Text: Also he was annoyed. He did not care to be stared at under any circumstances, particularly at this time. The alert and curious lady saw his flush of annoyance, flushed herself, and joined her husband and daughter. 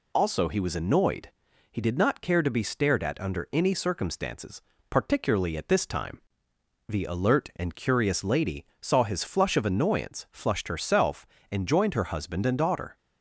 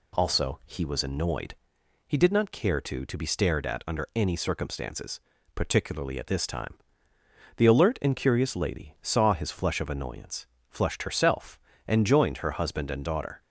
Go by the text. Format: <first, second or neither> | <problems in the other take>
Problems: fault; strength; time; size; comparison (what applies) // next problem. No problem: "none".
first | says "to" twice; at 3.0 s